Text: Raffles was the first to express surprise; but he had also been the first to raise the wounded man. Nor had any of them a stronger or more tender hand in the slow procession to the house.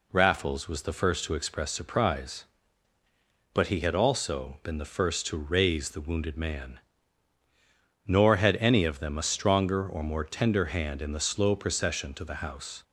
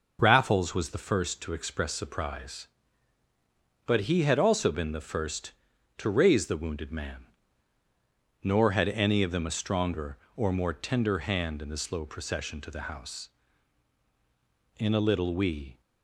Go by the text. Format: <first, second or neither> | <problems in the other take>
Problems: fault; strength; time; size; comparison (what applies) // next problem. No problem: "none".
first | goes on to say "In a little we"; noticeable; from 14.7 s on; 1.0 s long